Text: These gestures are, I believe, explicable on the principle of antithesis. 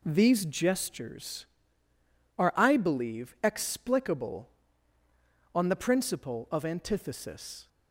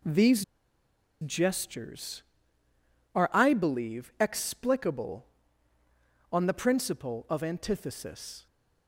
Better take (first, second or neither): first